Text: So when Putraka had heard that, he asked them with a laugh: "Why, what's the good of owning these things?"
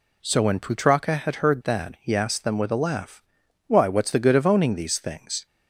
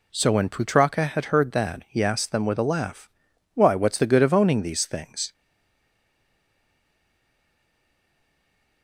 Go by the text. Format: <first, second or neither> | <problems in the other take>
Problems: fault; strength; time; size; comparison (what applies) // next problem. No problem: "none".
first | stays silent after the last word; strong; from 5.3 s on; 3.5 s long